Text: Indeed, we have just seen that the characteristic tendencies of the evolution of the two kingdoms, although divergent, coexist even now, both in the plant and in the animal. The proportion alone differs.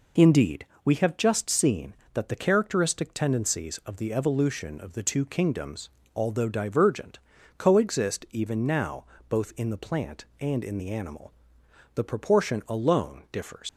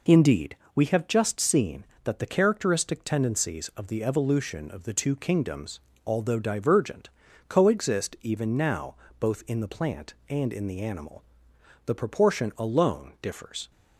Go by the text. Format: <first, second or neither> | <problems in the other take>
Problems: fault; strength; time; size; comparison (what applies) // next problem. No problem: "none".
second | leaves "differs" unfinished; at 13.6 s; 115 ms